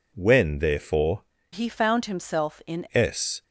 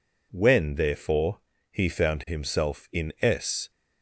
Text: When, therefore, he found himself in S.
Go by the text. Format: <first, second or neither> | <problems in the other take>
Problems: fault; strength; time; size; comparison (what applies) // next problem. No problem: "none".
second | changes voice from "he" to "in"; from 1.5 to 2.8 s; 1.3 s long